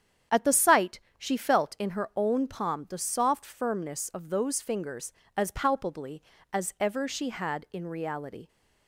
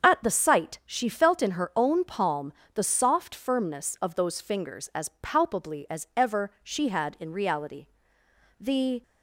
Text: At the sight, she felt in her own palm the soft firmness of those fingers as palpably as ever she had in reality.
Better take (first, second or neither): first